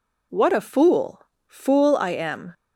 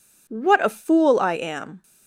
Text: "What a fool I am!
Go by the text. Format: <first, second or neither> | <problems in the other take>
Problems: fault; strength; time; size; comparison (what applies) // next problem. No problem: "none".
second | says "fool" twice; at 1.4 s